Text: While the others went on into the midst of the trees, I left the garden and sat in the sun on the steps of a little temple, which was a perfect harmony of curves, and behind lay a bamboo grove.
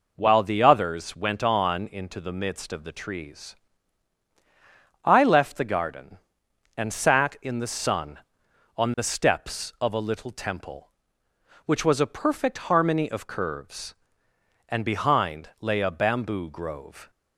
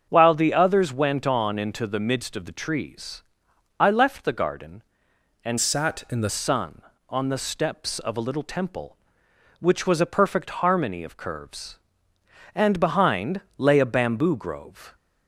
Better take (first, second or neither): first